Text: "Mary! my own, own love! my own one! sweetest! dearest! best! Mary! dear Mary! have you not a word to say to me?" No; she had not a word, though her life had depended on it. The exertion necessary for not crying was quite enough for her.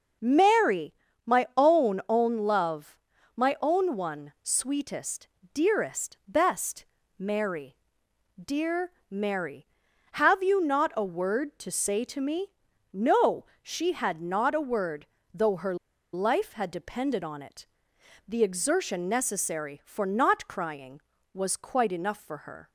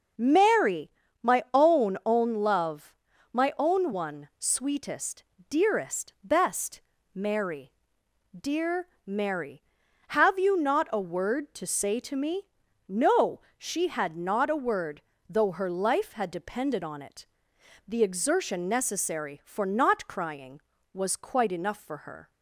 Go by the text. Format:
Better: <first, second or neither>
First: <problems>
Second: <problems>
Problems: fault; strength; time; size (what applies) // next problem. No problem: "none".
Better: second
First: pauses between "dear" and "Mary"; slight; at 8.9 s; 0.18 s long // pauses between "her" and "life"; at 15.7 s; 0.38 s long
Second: pauses between "dear" and "Mary"; slight; at 8.8 s; 0.18 s long